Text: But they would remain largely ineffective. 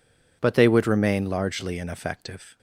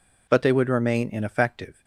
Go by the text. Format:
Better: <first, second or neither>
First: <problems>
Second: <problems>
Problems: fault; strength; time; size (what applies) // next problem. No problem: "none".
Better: first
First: none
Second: skips "largely"; at 1.0 s